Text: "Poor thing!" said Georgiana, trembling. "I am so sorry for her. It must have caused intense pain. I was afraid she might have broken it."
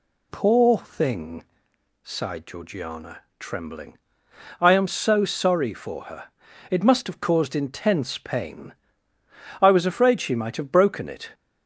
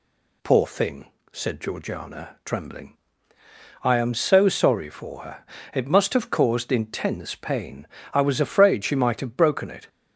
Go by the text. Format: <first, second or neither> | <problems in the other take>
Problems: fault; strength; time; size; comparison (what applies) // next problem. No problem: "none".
second | says "sighed" for "said"; at 2.0 s